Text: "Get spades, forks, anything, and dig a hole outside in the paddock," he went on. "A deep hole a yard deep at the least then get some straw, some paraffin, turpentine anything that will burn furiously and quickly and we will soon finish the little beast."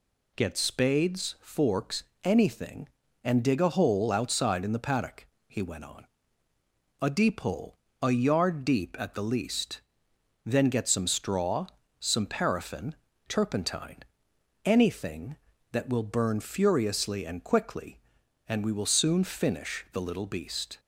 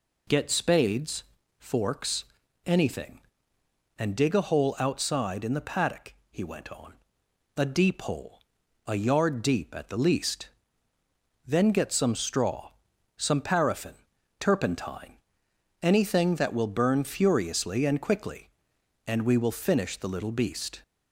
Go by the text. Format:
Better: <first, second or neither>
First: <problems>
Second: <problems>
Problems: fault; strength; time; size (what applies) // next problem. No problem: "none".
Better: first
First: pauses between "hole" and "a"; slight; at 7.7 s; 0.24 s long // pauses between "least" and "then"; noticeable; at 9.7 s; 0.64 s long // pauses between "turpentine" and "anything"; noticeable; at 13.9 s; 0.66 s long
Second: pauses between "hole" and "a"; noticeable; at 8.3 s; 0.52 s long // pauses between "least" and "then"; noticeable; at 10.4 s; 0.98 s long // pauses between "turpentine" and "anything"; noticeable; at 15.1 s; 0.64 s long // skips "soon"; at 19.6 s